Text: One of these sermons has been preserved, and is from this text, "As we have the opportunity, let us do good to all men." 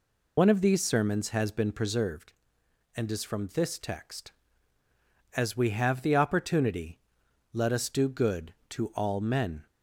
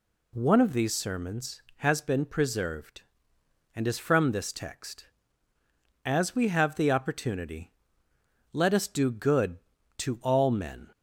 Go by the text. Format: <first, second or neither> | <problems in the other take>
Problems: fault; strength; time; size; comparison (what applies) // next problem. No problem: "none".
second | loses the start of "One"; at 0.3 s; 65 ms